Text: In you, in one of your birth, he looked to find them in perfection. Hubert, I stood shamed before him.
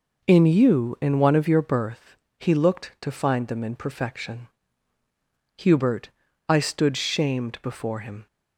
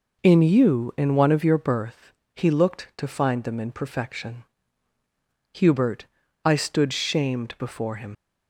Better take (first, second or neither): first